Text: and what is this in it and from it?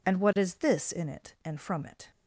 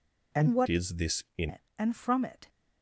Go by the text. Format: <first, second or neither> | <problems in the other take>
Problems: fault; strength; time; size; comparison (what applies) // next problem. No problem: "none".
first | changes voice from "is" to "in"; from 0.6 to 1.4 s; 0.8 s long